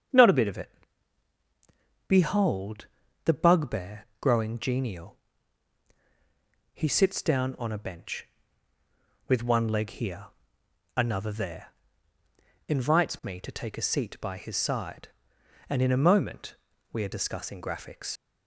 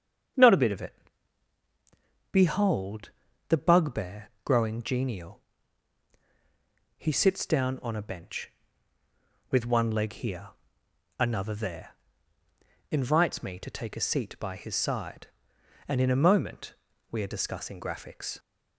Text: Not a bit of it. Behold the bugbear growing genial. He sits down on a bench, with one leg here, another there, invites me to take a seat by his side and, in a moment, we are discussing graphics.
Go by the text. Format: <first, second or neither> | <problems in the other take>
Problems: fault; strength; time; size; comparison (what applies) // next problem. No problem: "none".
second | starts louder than the rest; strong; until 2.5 s; 7.5 dB; strong in the second // pauses between "Behold" and "the"; at 2.8 s; 0.40 s long; also in the second // leaves "graphics" unfinished; at 18.1 s; 45 ms